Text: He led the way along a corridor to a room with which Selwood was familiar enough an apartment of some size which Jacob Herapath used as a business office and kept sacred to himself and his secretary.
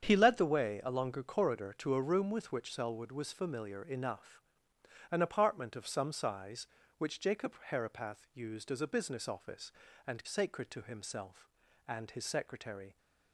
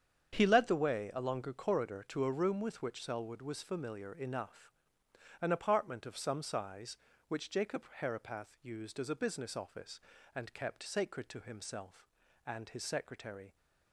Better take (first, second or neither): second